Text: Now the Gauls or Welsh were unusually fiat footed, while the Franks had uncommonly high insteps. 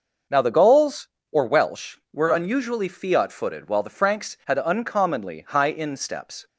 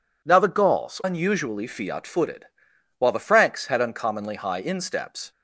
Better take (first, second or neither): first